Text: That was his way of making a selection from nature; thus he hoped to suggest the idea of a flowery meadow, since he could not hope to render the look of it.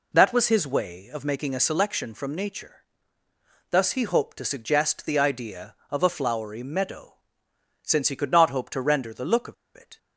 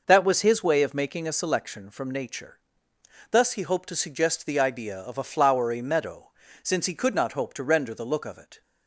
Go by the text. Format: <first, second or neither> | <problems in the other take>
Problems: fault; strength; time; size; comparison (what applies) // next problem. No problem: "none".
second | pauses between "of" and "it"; slight; at 9.5 s; 0.21 s long